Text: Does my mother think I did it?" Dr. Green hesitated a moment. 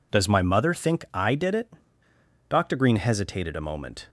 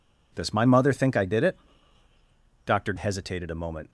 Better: first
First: none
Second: skips "Green"; at 2.9 s

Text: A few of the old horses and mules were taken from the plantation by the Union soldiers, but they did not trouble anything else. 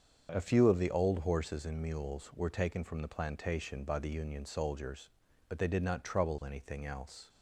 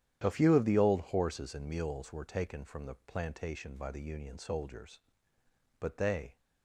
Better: first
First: starts louder than the rest; until 1.3 s; 7 dB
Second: starts louder than the rest; strong; until 1.2 s; 10.5 dB // stops before "did not trouble anything else"; at 6.3 s

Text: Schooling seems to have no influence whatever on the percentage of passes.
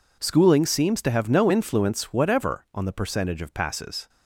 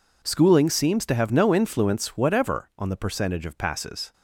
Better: neither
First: none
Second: none

